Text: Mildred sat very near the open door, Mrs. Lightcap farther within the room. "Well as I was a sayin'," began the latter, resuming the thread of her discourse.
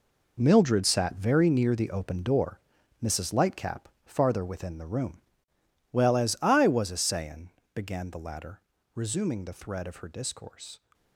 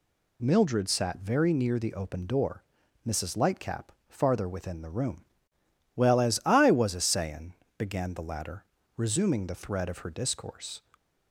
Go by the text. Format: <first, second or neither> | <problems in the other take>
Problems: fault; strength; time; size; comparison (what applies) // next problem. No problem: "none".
second | gets quieter; strong; throughout; 12 dB // pauses between "Lightcap" and "farther"; slight; at 3.8 s; 0.20 s long; slight in the second